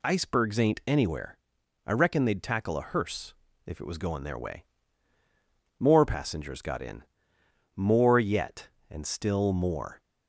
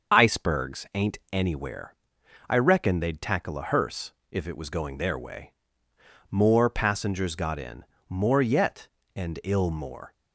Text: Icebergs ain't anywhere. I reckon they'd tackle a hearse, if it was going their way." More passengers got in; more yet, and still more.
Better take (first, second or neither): first